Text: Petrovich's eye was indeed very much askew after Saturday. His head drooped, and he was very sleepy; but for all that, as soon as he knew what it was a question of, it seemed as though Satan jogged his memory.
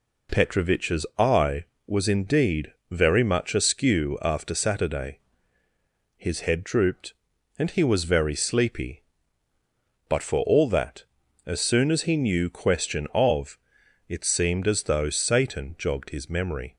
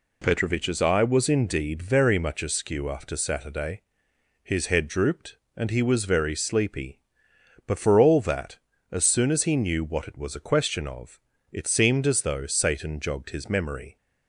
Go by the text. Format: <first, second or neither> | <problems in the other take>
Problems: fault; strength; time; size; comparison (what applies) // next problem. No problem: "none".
second | pauses between "indeed" and "very"; slight; at 2.7 s; 0.18 s long // skips "what it was a"; at 12.4 s